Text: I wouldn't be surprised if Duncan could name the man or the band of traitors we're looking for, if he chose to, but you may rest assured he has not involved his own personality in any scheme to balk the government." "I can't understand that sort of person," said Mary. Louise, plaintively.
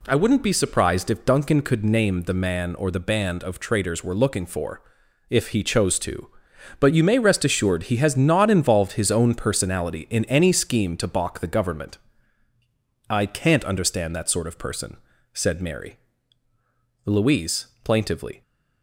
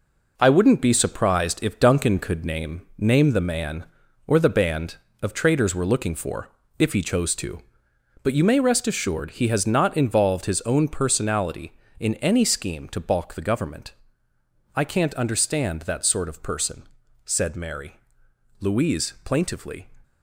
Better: first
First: none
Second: says "name" twice; at 2.9 s

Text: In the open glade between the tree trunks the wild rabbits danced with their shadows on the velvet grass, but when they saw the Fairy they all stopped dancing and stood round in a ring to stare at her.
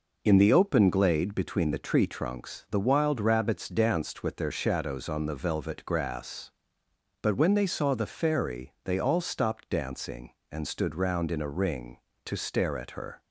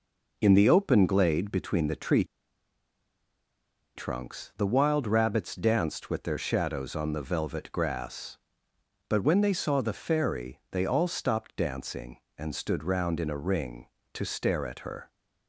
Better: first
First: none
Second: pauses between "tree" and "trunks"; strong; at 2.2 s; 1.7 s long

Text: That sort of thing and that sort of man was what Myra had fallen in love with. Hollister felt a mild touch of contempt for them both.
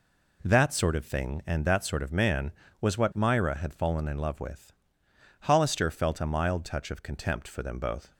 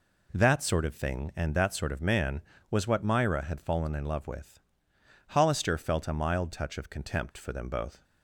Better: neither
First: none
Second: none

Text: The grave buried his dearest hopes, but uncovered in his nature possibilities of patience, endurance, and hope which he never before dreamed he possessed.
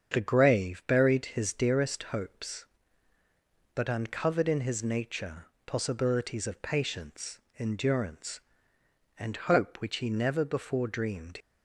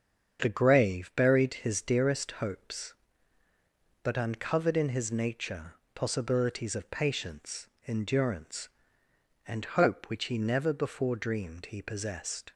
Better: second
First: starts louder than the rest; until 1.1 s; 7 dB // pauses between "nature" and "possibilities"; slight; at 5.4 s; 0.18 s long // stops before "he possessed"; at 11.4 s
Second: starts louder than the rest; until 1.4 s; 7 dB // pauses between "nature" and "possibilities"; slight; at 5.7 s; 0.18 s long

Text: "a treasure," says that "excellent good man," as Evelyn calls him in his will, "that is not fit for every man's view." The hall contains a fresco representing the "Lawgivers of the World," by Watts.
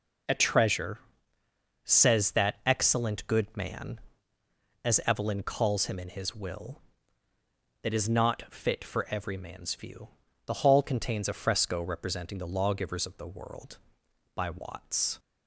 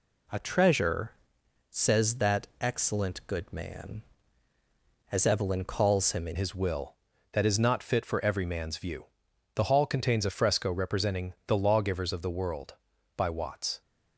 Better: first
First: none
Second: changes voice at "his"; from 6.3 s on; 7.5 s long

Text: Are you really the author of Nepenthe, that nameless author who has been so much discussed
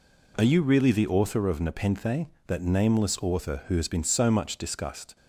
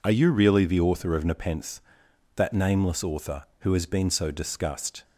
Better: first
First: none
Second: skips "much"; at 4.3 s

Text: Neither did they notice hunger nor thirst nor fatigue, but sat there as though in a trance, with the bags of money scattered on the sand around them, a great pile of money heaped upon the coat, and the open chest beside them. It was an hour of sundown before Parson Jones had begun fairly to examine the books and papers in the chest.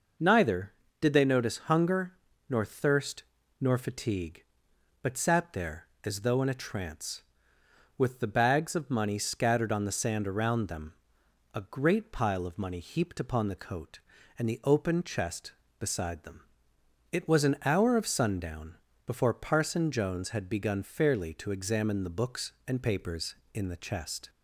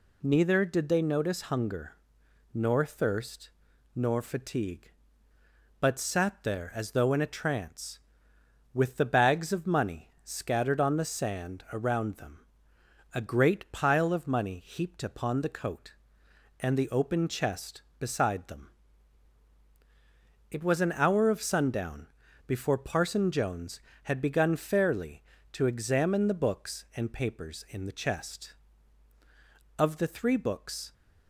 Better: first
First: pauses between "hunger" and "nor"; slight; at 2.1 s; 0.34 s long // pauses between "thirst" and "nor"; slight; at 3.2 s; 0.36 s long // pauses between "sundown" and "before"; slight; at 18.7 s; 0.30 s long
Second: pauses between "hunger" and "nor"; noticeable; at 1.9 s; 0.60 s long // pauses between "thirst" and "nor"; at 3.5 s; 0.44 s long // pauses between "sundown" and "before"; at 22.0 s; 0.40 s long // goes on to say "Of the three books"; noticeable; from 29.7 s on; 1.1 s long

